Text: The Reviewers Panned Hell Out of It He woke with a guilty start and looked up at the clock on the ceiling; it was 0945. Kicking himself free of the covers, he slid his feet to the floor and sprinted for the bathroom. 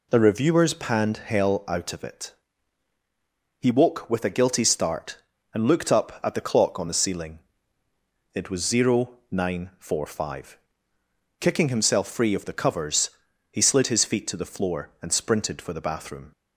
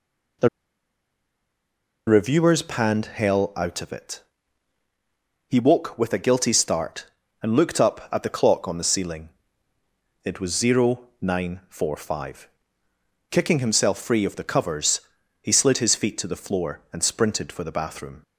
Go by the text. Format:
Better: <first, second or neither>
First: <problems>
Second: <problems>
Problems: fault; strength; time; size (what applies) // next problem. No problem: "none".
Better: first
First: pauses between "It" and "He"; strong; at 2.3 s; 1.2 s long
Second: pauses between "The" and "Reviewers"; strong; at 0.4 s; 1.5 s long // pauses between "It" and "He"; strong; at 4.2 s; 1.2 s long